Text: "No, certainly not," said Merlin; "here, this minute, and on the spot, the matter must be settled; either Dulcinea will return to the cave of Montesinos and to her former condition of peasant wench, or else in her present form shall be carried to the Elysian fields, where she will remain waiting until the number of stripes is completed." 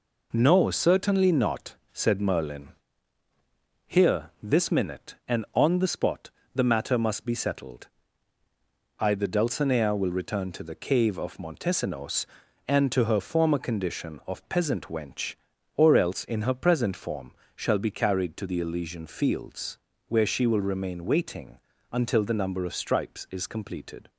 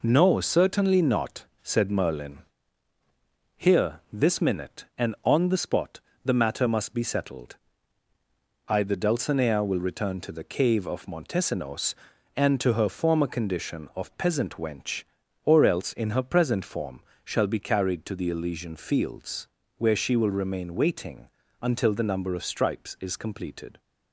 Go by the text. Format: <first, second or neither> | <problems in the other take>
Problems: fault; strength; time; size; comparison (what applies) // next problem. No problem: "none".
neither | pauses between "form" and "shall"; slight; the same in both // pauses between "waiting" and "until"; slight; the same in both